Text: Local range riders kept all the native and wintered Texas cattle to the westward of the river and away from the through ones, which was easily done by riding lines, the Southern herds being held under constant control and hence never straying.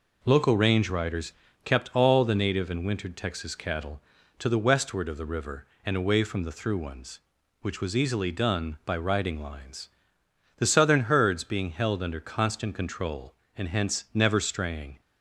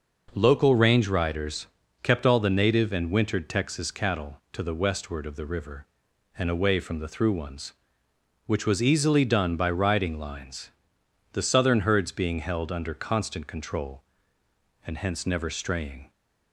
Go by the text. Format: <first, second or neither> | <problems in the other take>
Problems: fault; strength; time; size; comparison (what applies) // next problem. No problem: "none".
neither | pauses between "riders" and "kept"; the same in both